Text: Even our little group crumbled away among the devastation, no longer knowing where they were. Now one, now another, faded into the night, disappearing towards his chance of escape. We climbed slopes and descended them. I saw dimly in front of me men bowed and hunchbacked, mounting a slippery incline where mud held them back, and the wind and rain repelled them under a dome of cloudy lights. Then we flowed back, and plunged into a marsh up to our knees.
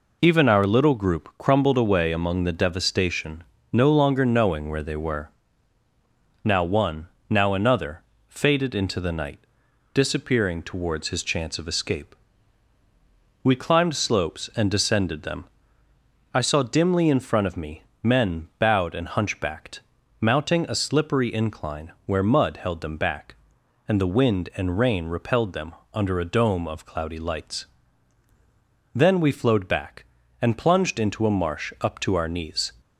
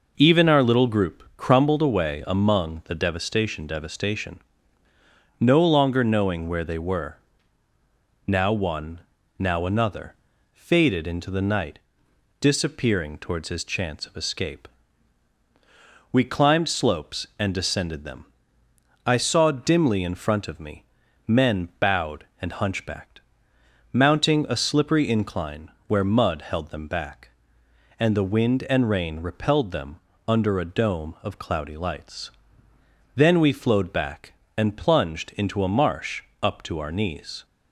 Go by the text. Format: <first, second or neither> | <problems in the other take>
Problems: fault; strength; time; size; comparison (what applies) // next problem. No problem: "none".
first | says "devastation" twice; at 3.6 s // pauses between "me" and "men"; at 20.8 s; 0.42 s long; slight in the first // pauses between "incline" and "where"; slight; at 25.7 s; 0.18 s long // pauses between "them" and "under"; slight; at 29.9 s; 0.30 s long; slight in the first // pauses between "marsh" and "up"; slight; at 36.2 s; 0.18 s long